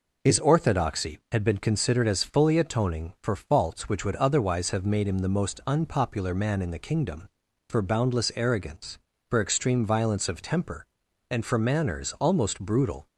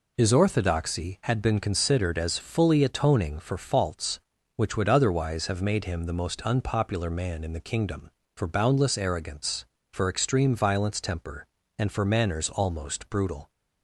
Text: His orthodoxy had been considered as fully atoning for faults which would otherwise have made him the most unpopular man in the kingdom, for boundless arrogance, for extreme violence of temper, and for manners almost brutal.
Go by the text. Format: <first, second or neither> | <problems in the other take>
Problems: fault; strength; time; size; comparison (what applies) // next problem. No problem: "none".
first | skips "of"; at 11.0 s